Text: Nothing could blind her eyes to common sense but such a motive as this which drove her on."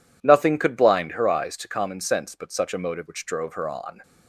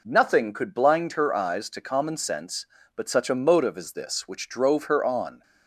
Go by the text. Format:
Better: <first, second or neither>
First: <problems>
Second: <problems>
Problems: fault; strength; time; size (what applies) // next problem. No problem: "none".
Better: second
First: skips "as this"; at 3.0 s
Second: none